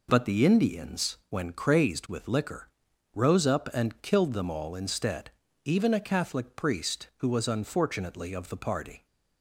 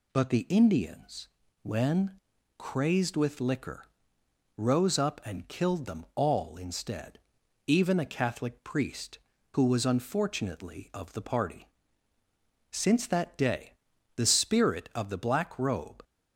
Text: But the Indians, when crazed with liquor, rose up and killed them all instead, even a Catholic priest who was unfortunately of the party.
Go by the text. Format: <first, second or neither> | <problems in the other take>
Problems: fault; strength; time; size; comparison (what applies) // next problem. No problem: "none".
first | pauses between "when" and "crazed"; at 2.1 s; 0.38 s long // goes on to say "Since that day the spirit of the Black Robe"; strong; from 12.7 s on; 3.3 s long